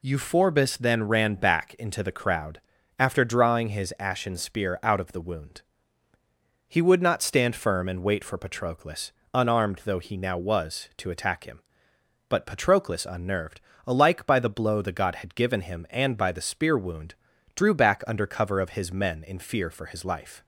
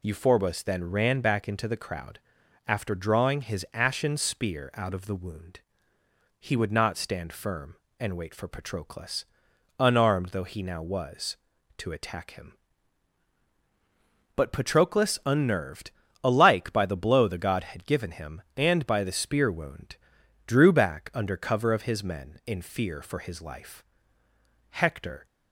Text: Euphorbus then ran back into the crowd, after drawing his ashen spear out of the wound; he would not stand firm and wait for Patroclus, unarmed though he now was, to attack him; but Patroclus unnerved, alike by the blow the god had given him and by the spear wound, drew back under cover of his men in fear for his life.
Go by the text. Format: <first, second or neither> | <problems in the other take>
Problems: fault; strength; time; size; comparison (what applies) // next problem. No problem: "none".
first | goes on to say "Hector"; from 24.7 s on; 0.56 s long